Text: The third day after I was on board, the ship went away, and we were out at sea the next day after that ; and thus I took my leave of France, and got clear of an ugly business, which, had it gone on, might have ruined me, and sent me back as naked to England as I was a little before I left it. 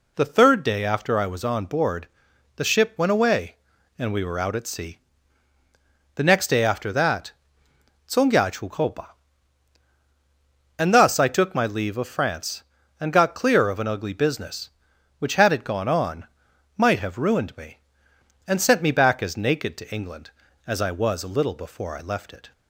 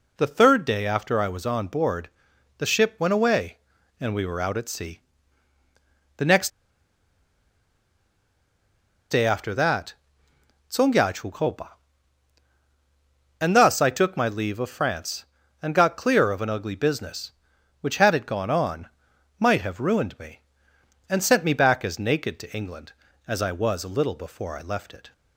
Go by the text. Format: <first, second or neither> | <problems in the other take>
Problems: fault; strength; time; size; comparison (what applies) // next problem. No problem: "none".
first | pauses between "sea" and "the"; at 4.9 s; 1.1 s long; also in the first // pauses between "next" and "day"; strong; at 6.4 s; 2.6 s long // pauses between "and" and "thus"; strong; at 11.0 s; 2.4 s long; strong in the first